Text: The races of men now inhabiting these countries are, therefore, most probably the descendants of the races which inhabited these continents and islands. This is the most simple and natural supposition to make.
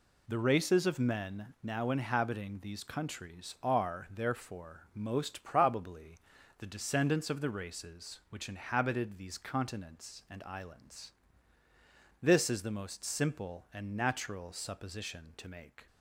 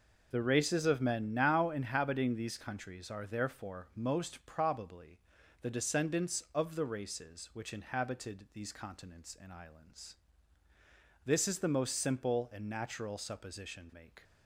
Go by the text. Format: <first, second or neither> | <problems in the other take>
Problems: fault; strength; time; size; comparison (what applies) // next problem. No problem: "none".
first | pauses between "probably" and "the"; at 5.1 s; 0.40 s long; also in the first // skips "to"; at 13.9 s